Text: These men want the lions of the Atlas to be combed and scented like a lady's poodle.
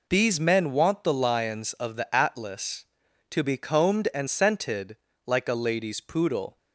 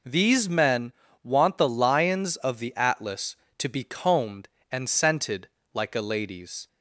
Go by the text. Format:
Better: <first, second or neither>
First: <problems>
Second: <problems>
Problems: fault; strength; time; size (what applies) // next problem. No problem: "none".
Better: first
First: pauses between "scented" and "like"; slight; at 4.9 s; 0.30 s long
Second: pauses between "men" and "want"; slight; at 0.9 s; 0.30 s long // pauses between "scented" and "like"; slight; at 5.4 s; 0.26 s long // stops before "poodle"; at 6.6 s